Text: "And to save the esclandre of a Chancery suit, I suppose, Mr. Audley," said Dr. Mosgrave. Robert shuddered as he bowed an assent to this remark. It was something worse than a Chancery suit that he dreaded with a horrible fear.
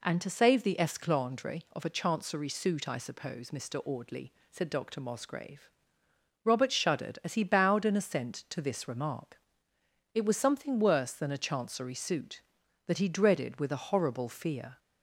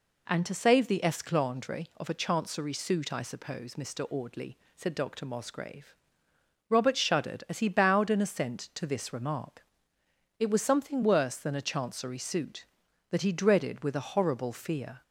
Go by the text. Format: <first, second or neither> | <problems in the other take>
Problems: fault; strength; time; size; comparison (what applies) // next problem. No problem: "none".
neither | none